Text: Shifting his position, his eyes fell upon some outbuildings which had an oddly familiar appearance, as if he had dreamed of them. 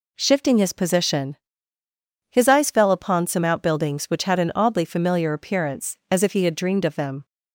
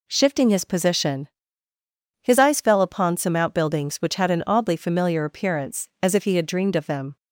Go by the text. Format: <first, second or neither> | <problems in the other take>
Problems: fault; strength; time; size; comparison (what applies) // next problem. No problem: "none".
neither | none